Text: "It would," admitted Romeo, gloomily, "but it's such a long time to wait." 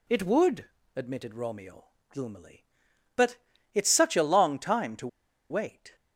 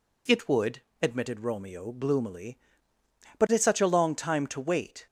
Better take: second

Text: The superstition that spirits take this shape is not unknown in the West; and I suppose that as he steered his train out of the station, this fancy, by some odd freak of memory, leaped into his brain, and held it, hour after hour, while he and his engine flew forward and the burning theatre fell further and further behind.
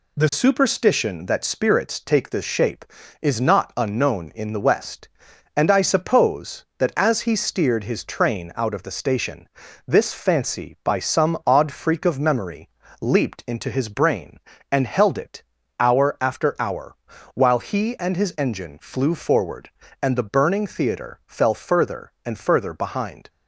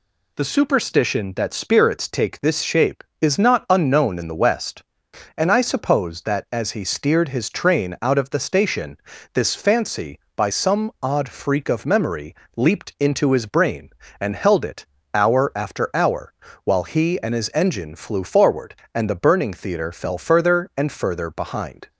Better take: neither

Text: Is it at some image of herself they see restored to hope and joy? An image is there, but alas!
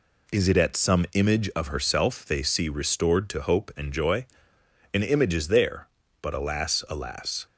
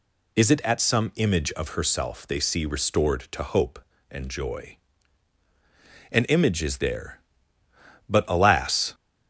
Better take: second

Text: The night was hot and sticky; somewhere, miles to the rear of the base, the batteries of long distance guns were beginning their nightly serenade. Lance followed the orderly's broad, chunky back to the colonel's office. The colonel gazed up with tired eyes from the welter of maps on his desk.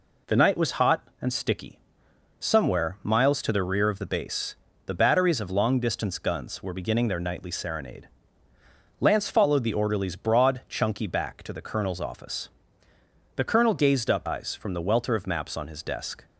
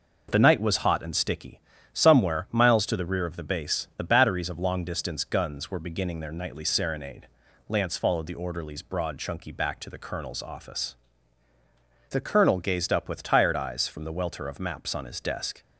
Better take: second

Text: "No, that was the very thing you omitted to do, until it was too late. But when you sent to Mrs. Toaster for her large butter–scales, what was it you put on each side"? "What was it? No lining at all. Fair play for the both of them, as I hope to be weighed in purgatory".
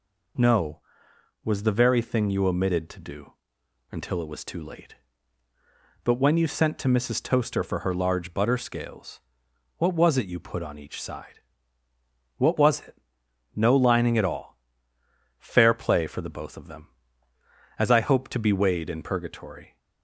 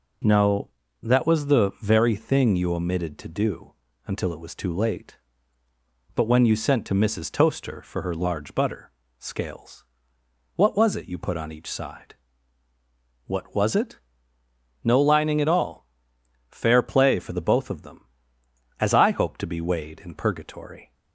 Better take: second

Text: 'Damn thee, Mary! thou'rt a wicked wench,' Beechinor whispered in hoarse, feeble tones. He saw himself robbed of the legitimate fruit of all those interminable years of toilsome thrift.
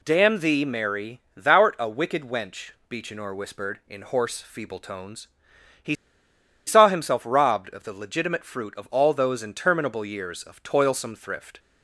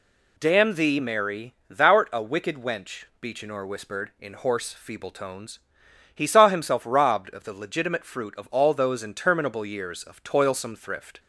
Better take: second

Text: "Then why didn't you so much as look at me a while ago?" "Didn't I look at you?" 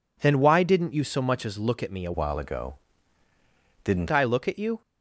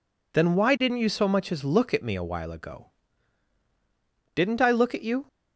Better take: second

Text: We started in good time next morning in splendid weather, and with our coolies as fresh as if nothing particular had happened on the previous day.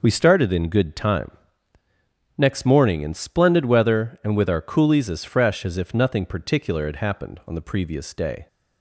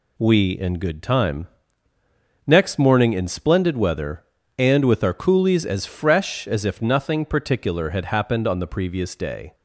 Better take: first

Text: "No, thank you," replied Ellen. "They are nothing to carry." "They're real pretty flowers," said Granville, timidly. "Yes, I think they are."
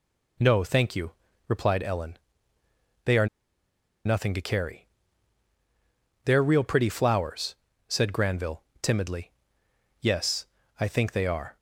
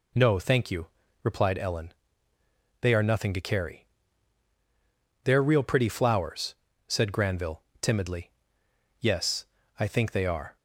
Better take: second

